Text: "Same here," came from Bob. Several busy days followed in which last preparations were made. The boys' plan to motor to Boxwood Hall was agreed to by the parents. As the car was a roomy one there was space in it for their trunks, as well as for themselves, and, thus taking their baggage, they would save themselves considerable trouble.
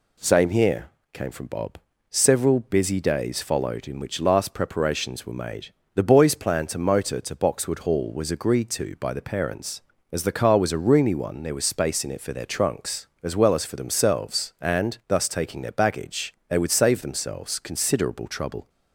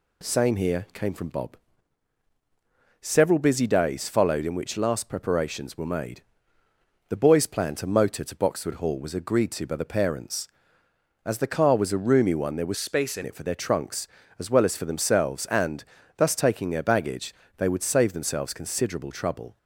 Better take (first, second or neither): first